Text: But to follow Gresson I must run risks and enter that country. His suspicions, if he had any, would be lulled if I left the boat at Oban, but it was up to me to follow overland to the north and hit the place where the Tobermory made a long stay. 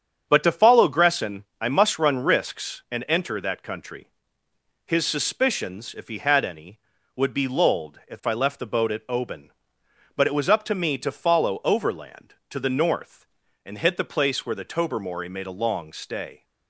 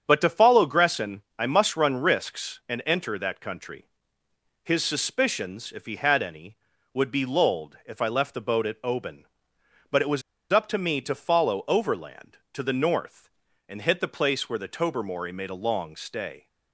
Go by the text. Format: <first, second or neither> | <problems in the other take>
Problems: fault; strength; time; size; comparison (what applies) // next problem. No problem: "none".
first | starts louder than the rest; strong; until 1.0 s; 7.5 dB; strong in the first // pauses between "Gresson" and "I"; slight; at 1.2 s; 0.16 s long; slight in the first // pauses between "was" and "up"; slight; at 10.2 s; 0.31 s long